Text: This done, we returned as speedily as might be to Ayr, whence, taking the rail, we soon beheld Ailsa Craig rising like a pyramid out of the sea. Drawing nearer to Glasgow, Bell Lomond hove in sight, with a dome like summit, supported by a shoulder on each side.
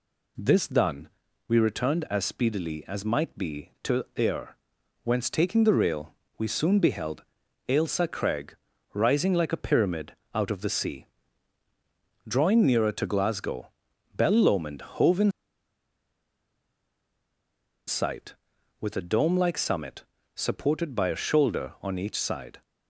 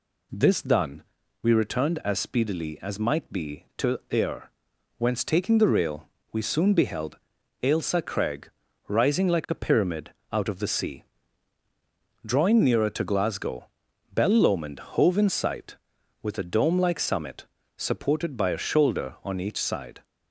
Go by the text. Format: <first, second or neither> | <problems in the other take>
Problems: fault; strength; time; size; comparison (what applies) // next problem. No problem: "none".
second | pauses between "beheld" and "Ailsa"; noticeable; at 7.2 s; 0.46 s long; noticeable in the second // pauses between "Craig" and "rising"; at 8.5 s; 0.38 s long; also in the second // pauses between "pyramid" and "out"; slight; at 10.1 s; 0.20 s long; slight in the second // pauses between "in" and "sight"; strong; at 15.3 s; 2.5 s long